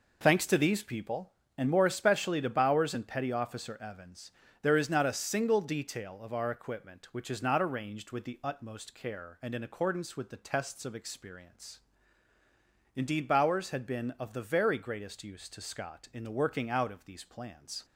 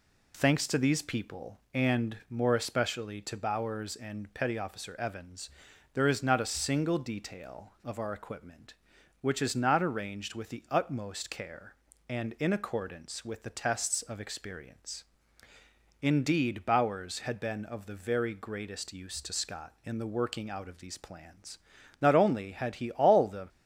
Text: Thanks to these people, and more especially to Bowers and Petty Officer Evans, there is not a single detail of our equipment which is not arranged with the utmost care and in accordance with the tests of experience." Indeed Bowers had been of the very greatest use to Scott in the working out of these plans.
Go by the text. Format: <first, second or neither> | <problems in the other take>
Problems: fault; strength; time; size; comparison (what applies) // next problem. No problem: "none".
first | goes on to say "Not only had he all the"; from 21.9 s on; 1.4 s long